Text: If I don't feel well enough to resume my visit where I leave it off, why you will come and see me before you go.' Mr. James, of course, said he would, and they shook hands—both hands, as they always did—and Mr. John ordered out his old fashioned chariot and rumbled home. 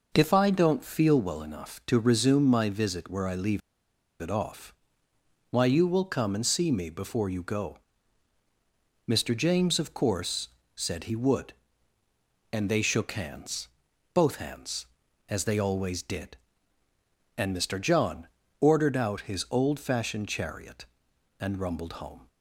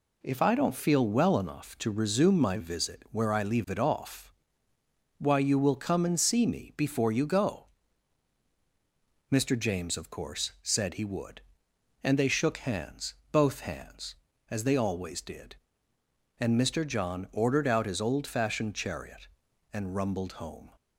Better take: second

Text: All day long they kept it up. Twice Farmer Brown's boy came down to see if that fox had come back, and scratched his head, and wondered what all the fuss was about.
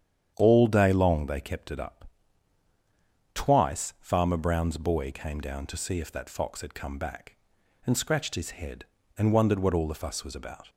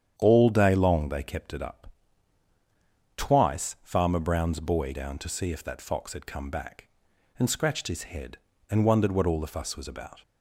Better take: first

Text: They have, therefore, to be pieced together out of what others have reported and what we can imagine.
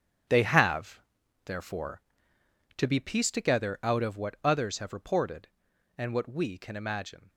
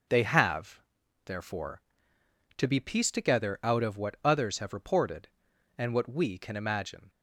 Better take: second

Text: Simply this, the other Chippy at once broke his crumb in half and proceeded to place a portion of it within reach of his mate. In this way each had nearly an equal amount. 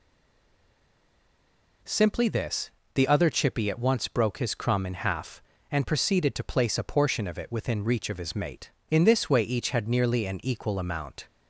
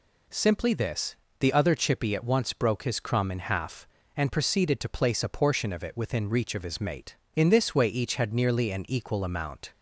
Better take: second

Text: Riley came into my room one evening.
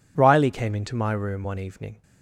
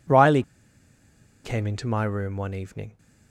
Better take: first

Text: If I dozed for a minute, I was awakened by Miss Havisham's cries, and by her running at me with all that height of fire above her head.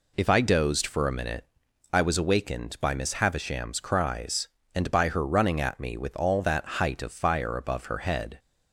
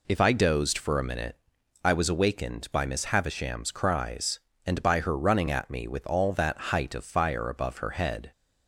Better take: neither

